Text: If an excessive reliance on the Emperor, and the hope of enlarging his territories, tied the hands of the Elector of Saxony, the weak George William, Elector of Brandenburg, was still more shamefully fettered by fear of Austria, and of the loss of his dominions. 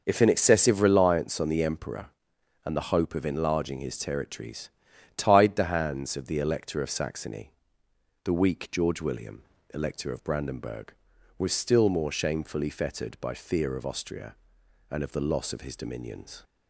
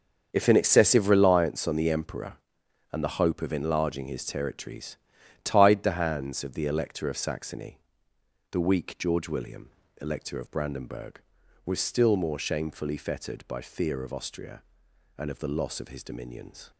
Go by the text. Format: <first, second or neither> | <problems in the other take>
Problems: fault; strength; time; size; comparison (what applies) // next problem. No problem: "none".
first | gets quieter; strong; throughout; 12 dB